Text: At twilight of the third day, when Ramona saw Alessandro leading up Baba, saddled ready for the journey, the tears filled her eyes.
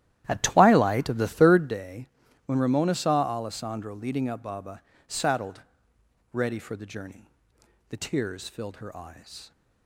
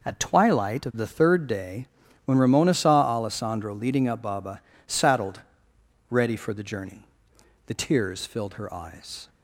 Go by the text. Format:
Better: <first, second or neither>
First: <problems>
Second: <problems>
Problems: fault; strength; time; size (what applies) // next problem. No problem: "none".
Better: second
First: starts louder than the rest; strong; until 1.8 s; 12.5 dB // pauses between "saddled" and "ready"; noticeable; at 5.6 s; 0.72 s long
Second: pauses between "saddled" and "ready"; noticeable; at 5.4 s; 0.70 s long